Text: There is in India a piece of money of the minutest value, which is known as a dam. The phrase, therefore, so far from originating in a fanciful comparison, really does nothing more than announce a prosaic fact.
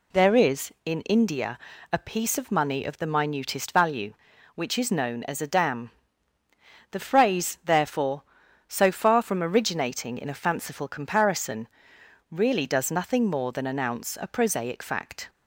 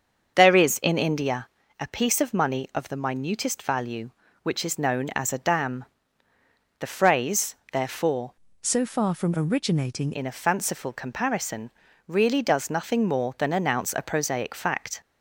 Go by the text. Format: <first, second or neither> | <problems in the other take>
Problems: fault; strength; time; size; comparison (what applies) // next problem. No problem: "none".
first | starts louder than the rest; until 1.3 s; 6.5 dB // pauses between "India" and "a"; slight; at 1.4 s; 0.32 s long; slight in the first // changes voice from "so" to "originating"; from 8.6 to 10.1 s; 1.5 s long